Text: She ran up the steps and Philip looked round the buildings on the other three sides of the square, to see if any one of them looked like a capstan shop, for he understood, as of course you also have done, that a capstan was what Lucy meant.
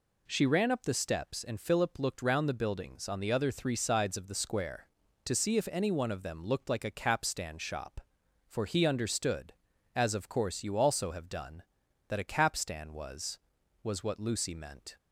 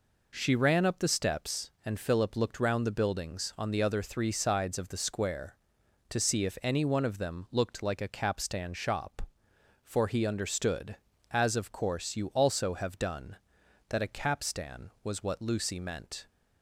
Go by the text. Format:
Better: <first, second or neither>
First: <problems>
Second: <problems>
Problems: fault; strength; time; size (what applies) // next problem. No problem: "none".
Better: second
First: says "was" twice; at 13.8 s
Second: none